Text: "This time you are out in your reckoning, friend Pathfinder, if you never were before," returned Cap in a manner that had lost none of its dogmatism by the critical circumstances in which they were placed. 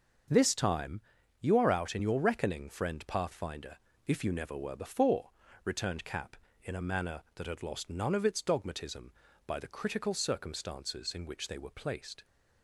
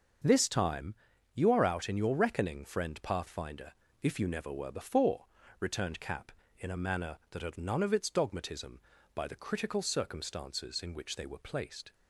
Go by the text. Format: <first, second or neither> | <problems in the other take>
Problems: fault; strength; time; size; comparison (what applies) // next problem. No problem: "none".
first | starts louder than the rest; until 1.6 s; 6.5 dB; also in the first // pauses between "time" and "you"; at 0.9 s; 0.40 s long; also in the first // skips "lost"; at 7.5 s